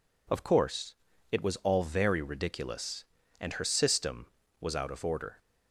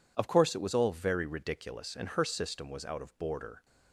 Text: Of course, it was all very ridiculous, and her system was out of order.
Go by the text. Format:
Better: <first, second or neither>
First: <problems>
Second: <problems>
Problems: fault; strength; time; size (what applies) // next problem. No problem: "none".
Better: first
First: none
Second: says "border" for "order"; at 3.1 s